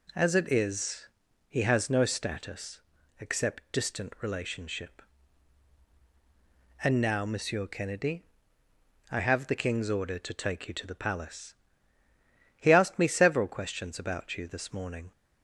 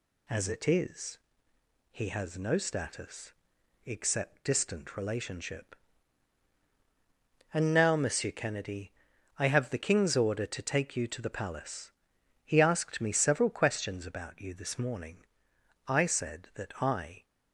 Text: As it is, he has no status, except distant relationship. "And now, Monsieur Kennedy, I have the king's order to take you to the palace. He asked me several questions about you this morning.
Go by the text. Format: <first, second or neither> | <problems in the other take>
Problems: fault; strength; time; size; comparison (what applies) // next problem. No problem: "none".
first | goes on to say "I said that I"; from 15.8 s on; 1.3 s long